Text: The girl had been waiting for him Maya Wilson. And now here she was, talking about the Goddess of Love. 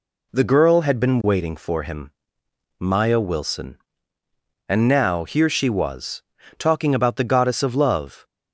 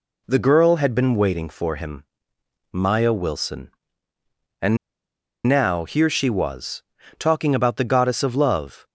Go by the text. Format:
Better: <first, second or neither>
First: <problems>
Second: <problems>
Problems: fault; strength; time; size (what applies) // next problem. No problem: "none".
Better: first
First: pauses between "him" and "Maya"; noticeable; at 2.1 s; 0.68 s long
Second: pauses between "him" and "Maya"; noticeable; at 2.0 s; 0.68 s long // pauses between "And" and "now"; noticeable; at 4.7 s; 0.69 s long